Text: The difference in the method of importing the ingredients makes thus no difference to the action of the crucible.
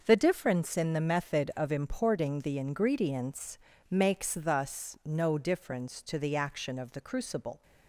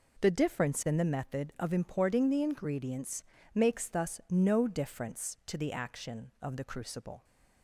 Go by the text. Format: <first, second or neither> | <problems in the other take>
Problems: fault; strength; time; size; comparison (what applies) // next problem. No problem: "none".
neither | pauses between "ingredients" and "makes"; slight; the same in both